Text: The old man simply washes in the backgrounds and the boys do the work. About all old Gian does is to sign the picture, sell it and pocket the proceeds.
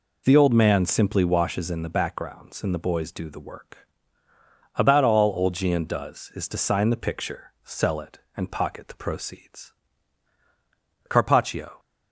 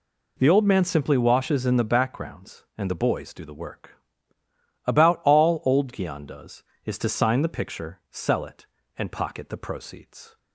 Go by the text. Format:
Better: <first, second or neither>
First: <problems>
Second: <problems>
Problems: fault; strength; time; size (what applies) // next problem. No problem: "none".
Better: second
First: goes on to say "Carpaccio"; noticeable; from 11.0 s on; 0.70 s long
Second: none